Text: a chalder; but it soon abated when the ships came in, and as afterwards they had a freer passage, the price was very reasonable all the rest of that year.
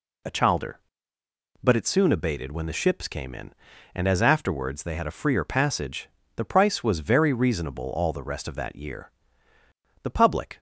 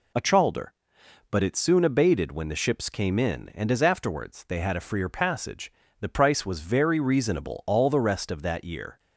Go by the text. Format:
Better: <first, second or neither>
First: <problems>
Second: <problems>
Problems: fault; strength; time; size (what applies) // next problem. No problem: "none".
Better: second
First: goes on to say "The public"; from 10.0 s on; 0.56 s long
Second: none